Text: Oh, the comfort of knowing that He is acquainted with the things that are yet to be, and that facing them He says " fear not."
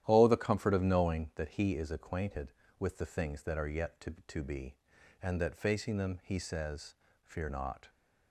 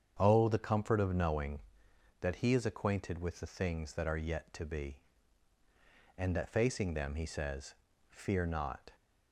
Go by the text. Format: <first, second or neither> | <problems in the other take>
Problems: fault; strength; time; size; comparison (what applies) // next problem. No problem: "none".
second | starts louder than the rest; strong; until 1.0 s; 11.5 dB; strong in the second // says "to" twice; at 4.2 s